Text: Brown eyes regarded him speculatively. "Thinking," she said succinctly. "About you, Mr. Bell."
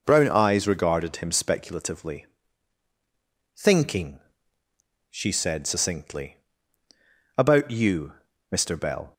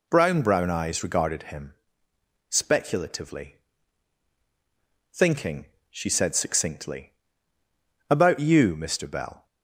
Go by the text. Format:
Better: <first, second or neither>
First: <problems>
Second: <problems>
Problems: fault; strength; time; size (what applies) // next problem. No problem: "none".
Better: first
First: none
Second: says "Brown" twice; at 0.4 s // pauses between "him" and "speculatively"; noticeable; at 1.7 s; 0.76 s long